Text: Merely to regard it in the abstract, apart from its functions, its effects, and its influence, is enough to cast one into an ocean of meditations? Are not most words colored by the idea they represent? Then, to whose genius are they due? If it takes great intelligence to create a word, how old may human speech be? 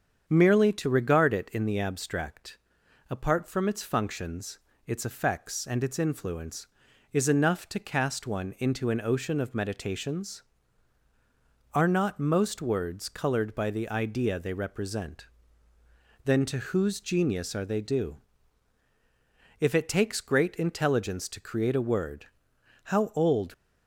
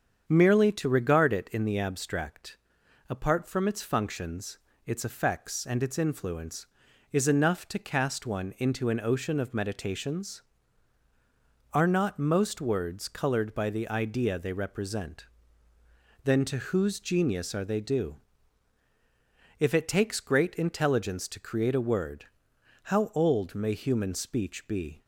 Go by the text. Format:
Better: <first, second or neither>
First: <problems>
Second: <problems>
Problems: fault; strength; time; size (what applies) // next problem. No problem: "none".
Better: second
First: starts louder than the rest; strong; until 1.2 s; 7.5 dB // stops before "may human speech be"; at 23.5 s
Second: starts louder than the rest; strong; until 1.2 s; 7.5 dB